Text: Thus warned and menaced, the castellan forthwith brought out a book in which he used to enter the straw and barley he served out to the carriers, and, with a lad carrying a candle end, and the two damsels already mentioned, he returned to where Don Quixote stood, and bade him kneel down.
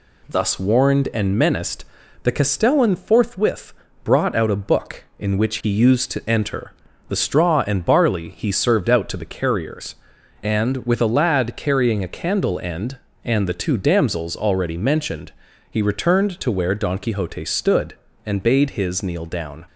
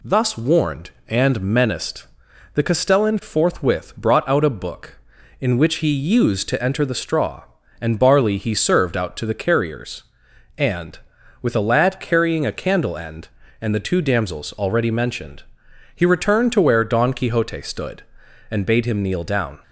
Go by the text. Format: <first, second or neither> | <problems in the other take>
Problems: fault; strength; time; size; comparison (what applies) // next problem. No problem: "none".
second | pauses between "forthwith" and "brought"; slight; at 3.7 s; 0.30 s long // pauses between "enter" and "the"; slight; at 6.7 s; 0.36 s long // says "his" for "him"; at 18.7 s